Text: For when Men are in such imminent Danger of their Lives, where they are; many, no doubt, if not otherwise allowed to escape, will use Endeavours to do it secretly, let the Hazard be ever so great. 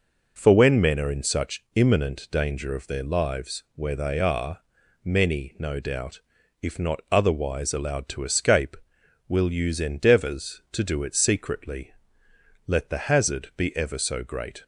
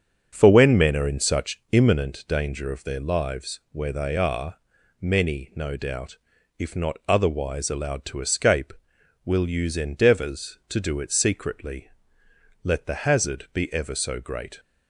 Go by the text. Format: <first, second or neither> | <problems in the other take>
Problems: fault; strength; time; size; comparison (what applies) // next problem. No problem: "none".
first | starts louder than the rest; until 2.1 s; 6.5 dB